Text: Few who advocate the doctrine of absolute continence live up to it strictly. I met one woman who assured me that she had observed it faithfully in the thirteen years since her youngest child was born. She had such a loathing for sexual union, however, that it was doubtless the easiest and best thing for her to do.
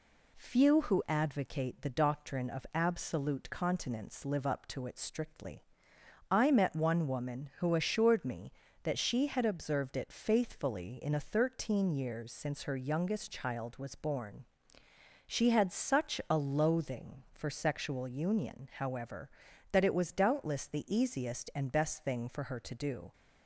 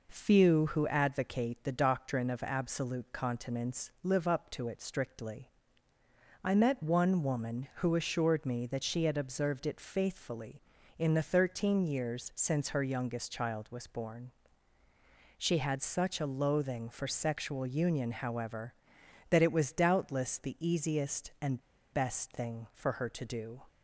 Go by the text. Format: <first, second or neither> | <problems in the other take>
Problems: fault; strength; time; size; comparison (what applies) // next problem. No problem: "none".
first | pauses between "and" and "best"; slight; at 21.6 s; 0.30 s long